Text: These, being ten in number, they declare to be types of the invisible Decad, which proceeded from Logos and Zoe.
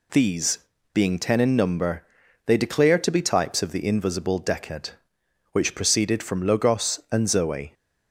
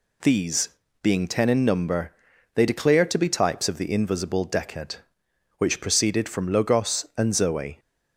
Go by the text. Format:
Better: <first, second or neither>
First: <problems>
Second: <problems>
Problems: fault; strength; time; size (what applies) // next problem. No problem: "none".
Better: neither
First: none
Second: none